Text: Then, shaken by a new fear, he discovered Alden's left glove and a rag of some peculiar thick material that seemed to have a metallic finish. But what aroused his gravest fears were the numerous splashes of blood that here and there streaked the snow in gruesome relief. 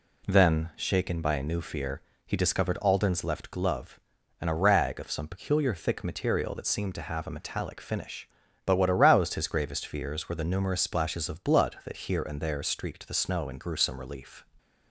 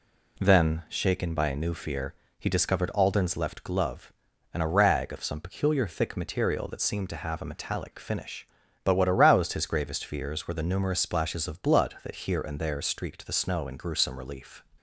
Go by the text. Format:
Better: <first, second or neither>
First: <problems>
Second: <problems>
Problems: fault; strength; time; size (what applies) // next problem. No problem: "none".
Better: neither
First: none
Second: none